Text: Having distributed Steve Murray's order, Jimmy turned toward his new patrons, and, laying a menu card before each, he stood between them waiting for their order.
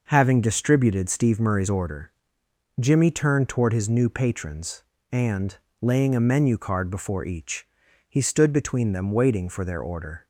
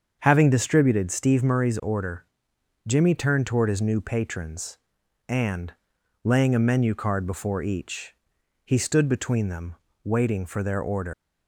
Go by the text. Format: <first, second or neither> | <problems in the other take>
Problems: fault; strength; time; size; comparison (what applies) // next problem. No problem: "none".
first | starts louder than the rest; until 1.2 s; 7 dB // pauses between "them" and "waiting"; slight; at 9.7 s; 0.30 s long // leaves "order" unfinished; at 11.1 s; 155 ms